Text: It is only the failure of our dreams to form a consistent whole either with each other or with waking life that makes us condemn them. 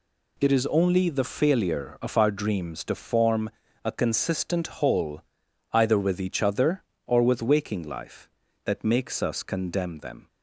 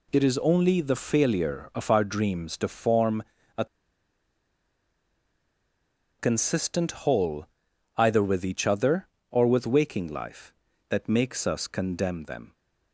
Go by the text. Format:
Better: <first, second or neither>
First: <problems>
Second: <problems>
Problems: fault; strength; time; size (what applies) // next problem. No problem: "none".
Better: first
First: pauses between "form" and "a"; slight; at 3.4 s; 0.36 s long // pauses between "whole" and "either"; noticeable; at 5.2 s; 0.50 s long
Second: pauses between "form" and "a"; slight; at 3.2 s; 0.36 s long // pauses between "a" and "consistent"; strong; at 3.6 s; 2.5 s long // pauses between "whole" and "either"; noticeable; at 7.4 s; 0.50 s long